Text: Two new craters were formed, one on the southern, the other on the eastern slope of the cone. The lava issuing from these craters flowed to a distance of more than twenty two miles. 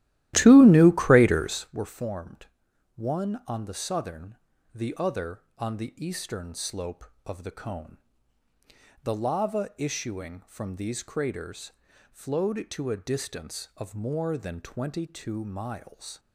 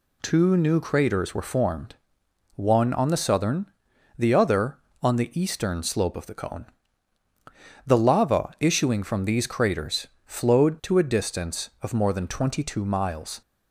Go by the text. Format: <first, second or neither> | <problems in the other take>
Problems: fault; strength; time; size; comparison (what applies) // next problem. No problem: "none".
second | starts louder than the rest; strong; until 1.8 s; 14.5 dB // pauses between "craters" and "flowed"; at 11.7 s; 0.40 s long; slight in the second